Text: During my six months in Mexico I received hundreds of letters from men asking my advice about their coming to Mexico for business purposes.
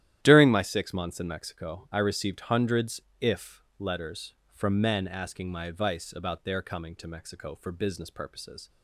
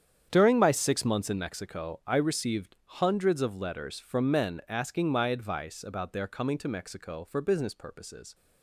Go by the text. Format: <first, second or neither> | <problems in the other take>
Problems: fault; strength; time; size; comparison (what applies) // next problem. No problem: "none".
second | starts louder than the rest; strong; until 1.2 s; 12 dB; strong in the second // says "if" for "of"; at 3.2 s